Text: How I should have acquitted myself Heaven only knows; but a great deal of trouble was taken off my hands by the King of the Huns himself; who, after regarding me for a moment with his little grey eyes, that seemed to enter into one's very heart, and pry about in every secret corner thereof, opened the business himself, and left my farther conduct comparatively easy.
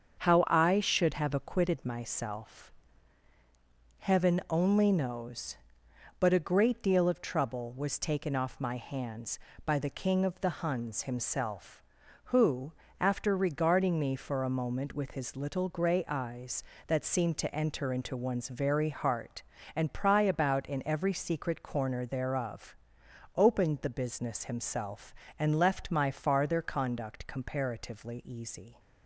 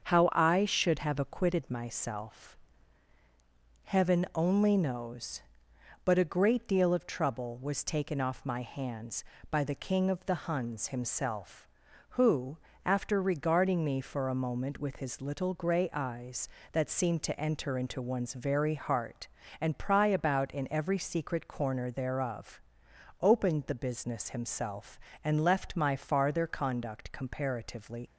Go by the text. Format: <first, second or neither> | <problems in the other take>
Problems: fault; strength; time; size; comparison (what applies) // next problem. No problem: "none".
first | starts louder than the rest; until 1.1 s; 7 dB; also in the first // pauses between "myself" and "Heaven"; strong; at 2.5 s; 1.2 s long; strong in the first // stops before "easy"; at 28.0 s